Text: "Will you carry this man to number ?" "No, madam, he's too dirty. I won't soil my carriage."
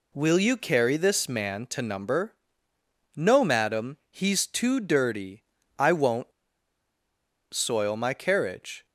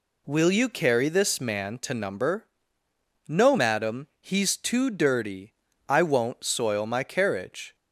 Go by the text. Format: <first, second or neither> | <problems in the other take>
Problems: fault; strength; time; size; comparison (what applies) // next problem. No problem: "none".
second | pauses between "won't" and "soil"; at 6.3 s; 1.2 s long